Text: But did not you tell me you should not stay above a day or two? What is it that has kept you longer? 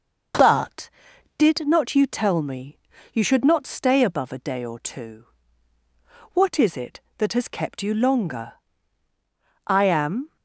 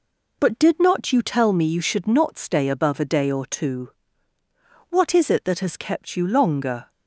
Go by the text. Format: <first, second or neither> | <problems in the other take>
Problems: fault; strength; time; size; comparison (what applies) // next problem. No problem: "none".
second | starts louder than the rest; noticeable; until 1.8 s; 6 dB // pauses between "me" and "you"; slight; at 2.7 s; 0.36 s long // goes on to say "I am"; noticeable; from 9.6 s on; 0.70 s long